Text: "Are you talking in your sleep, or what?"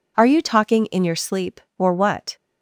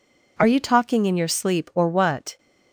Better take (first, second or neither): neither